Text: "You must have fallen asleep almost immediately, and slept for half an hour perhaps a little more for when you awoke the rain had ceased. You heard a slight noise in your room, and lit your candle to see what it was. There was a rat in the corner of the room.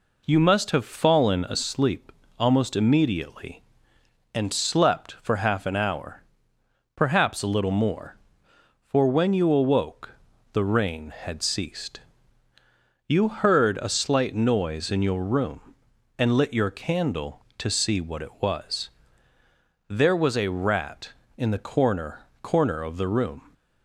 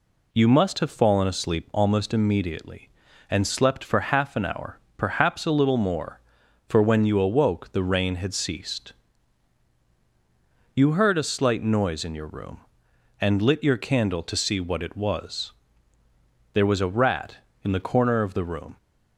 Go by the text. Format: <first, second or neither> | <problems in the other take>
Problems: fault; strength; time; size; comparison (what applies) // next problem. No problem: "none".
second | pauses between "asleep" and "almost"; slight; at 2.1 s; 0.28 s long // pauses between "hour" and "perhaps"; noticeable; at 6.2 s; 0.74 s long; slight in the second // pauses between "awoke" and "the"; at 10.1 s; 0.42 s long // says "corner" twice; at 22.4 s